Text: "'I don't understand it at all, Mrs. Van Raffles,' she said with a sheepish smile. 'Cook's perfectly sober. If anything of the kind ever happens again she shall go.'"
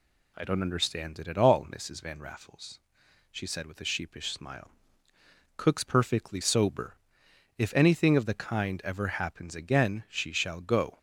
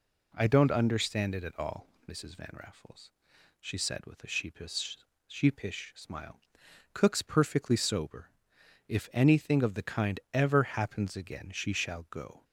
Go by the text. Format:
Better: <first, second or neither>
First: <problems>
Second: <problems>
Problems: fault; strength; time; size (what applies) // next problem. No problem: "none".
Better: first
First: none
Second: says "sheepish" twice; at 5.2 s